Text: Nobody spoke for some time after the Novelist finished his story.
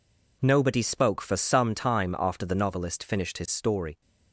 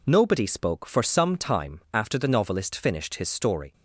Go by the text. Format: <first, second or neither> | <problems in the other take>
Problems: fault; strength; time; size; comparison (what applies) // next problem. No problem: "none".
neither | none